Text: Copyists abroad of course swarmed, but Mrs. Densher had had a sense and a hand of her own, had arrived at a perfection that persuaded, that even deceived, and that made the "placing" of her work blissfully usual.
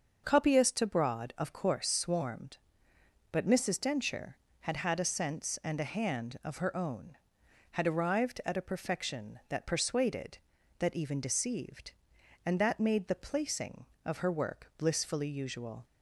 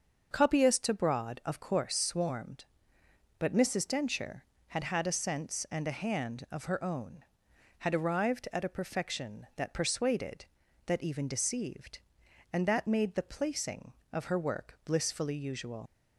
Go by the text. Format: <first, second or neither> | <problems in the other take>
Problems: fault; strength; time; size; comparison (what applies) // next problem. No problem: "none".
first | starts louder than the rest; until 1.3 s; 6.5 dB; also in the first // leaves "usual" unfinished; at 15.8 s; 60 ms